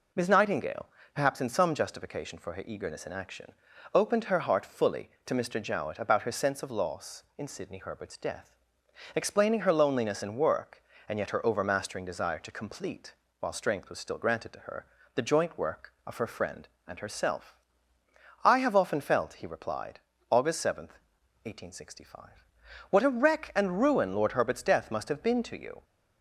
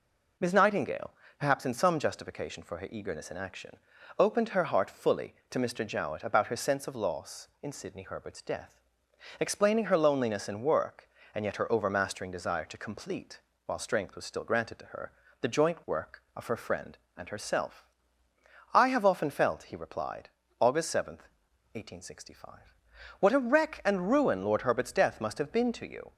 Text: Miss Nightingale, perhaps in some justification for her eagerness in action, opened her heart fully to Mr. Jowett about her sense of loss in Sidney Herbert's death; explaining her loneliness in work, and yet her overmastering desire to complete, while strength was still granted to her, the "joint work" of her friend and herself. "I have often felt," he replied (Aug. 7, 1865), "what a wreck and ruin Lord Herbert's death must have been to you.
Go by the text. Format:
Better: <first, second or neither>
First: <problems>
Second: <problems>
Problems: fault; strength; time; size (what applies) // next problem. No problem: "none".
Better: neither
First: none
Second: none